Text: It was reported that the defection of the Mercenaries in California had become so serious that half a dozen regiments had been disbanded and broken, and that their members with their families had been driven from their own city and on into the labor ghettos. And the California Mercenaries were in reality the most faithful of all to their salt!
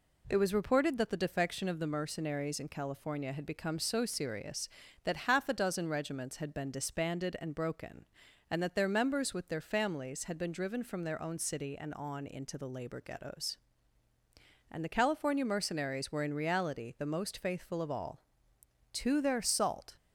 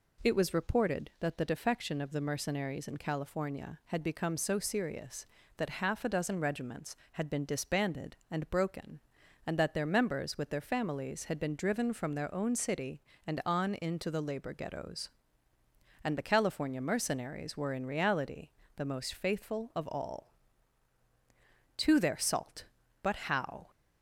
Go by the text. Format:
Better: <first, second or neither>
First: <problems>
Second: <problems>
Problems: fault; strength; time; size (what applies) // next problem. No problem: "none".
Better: first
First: none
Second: pauses between "reality" and "the"; slight; at 18.4 s; 0.26 s long // goes on to say "But how"; noticeable; from 23.0 s on; 0.68 s long